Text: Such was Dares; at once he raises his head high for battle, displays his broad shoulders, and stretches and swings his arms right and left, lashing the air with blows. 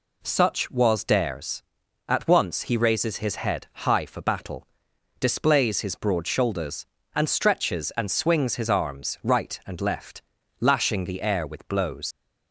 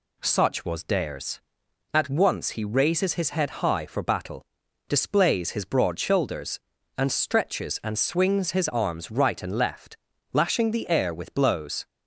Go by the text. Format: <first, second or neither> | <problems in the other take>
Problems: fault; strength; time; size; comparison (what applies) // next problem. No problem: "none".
second | leaves "blows" unfinished; at 12.1 s; 100 ms